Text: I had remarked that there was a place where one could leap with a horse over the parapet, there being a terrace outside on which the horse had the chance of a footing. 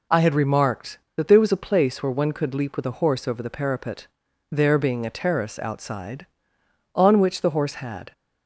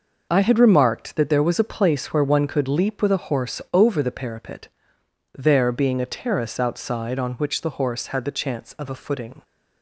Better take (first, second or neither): second